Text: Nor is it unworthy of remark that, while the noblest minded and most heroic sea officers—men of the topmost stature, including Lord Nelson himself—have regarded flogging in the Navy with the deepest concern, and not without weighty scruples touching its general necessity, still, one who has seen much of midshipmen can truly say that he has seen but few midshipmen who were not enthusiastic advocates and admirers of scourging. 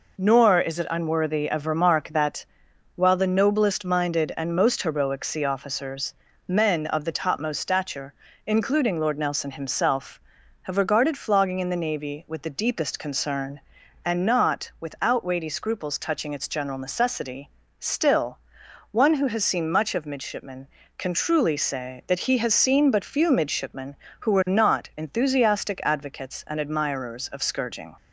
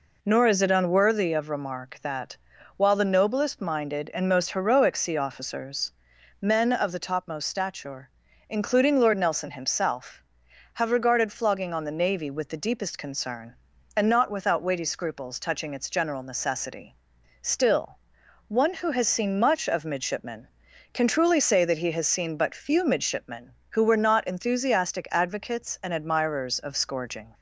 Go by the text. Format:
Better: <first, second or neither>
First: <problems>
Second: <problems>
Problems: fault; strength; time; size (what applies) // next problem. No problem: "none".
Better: first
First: none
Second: says "on" for "in"; at 11.7 s